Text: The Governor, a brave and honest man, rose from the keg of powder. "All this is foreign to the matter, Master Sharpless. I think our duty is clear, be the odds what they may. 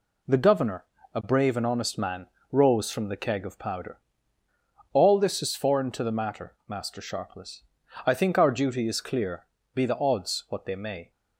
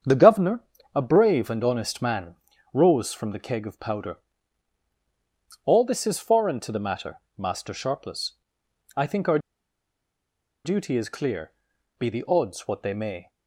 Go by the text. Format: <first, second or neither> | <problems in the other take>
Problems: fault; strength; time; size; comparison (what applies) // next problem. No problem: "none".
first | starts louder than the rest; strong; until 1.3 s; 7.5 dB // pauses between "our" and "duty"; strong; at 9.3 s; 1.2 s long